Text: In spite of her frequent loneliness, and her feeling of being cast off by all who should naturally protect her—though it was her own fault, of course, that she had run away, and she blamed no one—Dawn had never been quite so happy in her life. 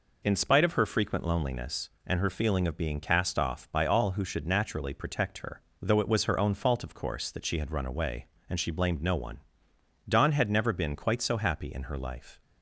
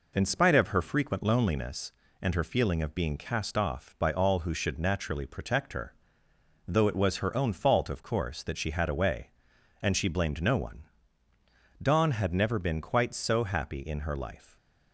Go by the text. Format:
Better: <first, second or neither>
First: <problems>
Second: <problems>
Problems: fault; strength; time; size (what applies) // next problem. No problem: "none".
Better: first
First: none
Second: skips "run"; at 8.8 s